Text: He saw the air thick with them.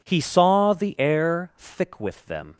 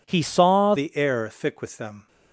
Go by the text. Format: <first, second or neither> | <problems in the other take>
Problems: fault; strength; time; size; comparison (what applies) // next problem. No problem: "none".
first | changes voice at "the"; from 0.7 s on; 1.3 s long